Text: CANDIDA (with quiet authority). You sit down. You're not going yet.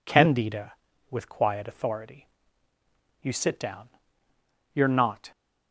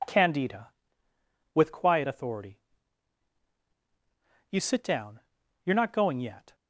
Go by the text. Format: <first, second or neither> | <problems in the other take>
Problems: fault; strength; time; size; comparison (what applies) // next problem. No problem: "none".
second | stops before "going yet"; at 5.3 s